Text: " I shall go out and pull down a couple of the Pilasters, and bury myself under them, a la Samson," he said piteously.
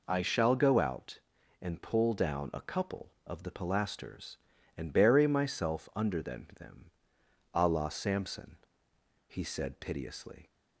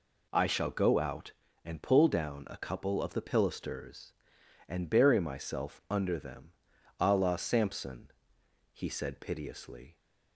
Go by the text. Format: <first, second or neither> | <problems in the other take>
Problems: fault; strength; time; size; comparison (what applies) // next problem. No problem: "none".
second | says "them" twice; at 6.5 s